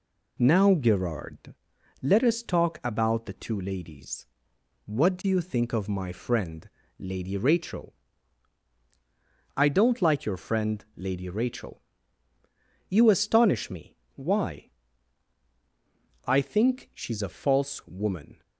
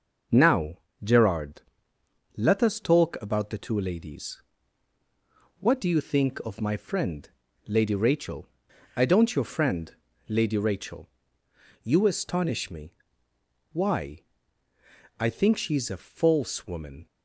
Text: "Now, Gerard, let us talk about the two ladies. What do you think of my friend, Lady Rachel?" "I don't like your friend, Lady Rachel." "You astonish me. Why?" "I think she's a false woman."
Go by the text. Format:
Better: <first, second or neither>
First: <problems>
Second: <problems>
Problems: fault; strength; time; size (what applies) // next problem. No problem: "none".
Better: first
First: none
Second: skips "like"; at 9.3 s